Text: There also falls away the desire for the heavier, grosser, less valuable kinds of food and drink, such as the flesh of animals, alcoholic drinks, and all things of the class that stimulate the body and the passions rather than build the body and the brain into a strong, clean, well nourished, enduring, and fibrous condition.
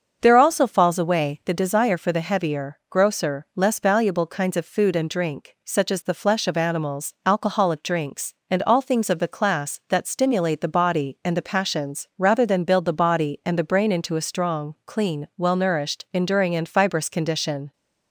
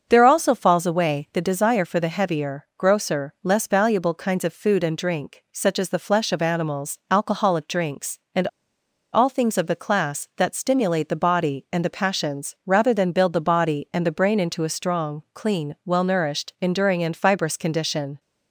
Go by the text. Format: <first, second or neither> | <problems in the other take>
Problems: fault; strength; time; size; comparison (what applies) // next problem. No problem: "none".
first | starts louder than the rest; until 1.0 s; 6.5 dB; also in the first // pauses between "and" and "all"; noticeable; at 8.4 s; 0.66 s long